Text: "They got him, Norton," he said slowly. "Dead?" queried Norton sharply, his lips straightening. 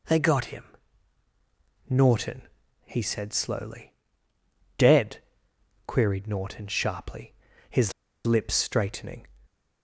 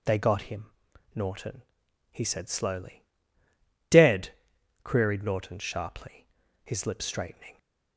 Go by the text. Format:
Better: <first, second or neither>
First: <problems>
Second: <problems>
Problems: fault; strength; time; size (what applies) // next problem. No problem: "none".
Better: second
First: pauses between "his" and "lips"; slight; at 7.9 s; 0.32 s long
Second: none